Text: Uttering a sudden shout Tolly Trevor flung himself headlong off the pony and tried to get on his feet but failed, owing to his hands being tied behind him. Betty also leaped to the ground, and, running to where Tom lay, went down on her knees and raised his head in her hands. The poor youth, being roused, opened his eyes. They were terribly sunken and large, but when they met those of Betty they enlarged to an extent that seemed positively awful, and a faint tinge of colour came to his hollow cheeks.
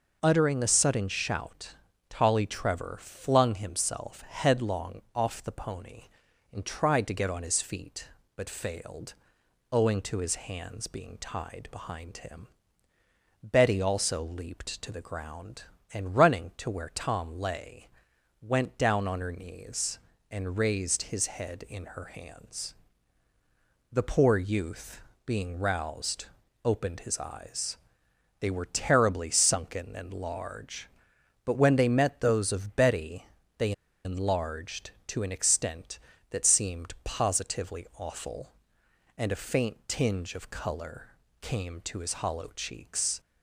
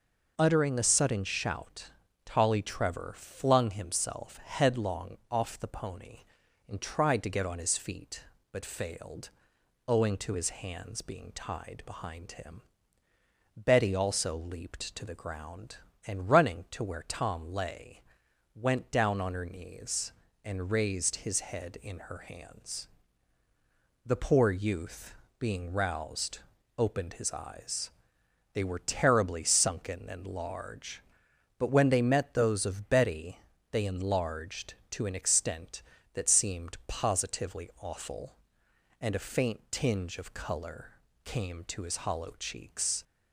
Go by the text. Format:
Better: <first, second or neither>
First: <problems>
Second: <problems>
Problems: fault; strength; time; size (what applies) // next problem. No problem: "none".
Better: second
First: pauses between "shout" and "Tolly"; slight; at 1.7 s; 0.34 s long // pauses between "headlong" and "off"; slight; at 4.9 s; 0.16 s long // pauses between "Betty" and "they"; slight; at 33.2 s; 0.32 s long // pauses between "they" and "enlarged"; slight; at 33.7 s; 0.33 s long // pauses between "colour" and "came"; slight; at 41.0 s; 0.32 s long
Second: pauses between "shout" and "Tolly"; slight; at 1.9 s; 0.34 s long // pauses between "headlong" and "off"; slight; at 5.1 s; 0.16 s long // pauses between "Betty" and "they"; slight; at 33.3 s; 0.32 s long // pauses between "colour" and "came"; slight; at 40.9 s; 0.32 s long